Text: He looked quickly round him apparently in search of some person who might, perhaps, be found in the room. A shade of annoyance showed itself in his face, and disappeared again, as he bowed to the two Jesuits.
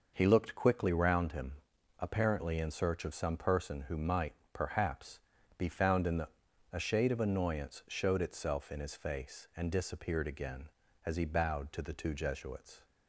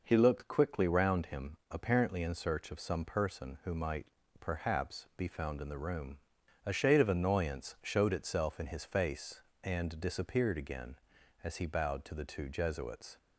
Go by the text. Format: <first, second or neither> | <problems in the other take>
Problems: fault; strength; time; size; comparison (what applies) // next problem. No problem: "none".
second | pauses between "him" and "apparently"; noticeable; at 1.5 s; 0.46 s long; slight in the second // skips "room"; at 6.5 s